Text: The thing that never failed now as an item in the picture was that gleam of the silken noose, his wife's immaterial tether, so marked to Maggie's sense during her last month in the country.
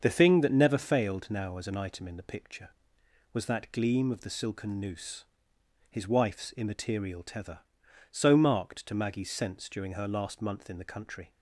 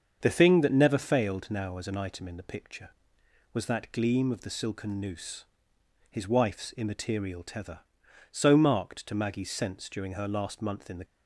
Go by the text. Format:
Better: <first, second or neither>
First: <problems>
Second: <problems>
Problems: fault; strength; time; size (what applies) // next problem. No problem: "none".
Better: first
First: starts louder than the rest; until 1.0 s; 7 dB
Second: starts louder than the rest; until 1.2 s; 7 dB // stops before "country"; at 11.0 s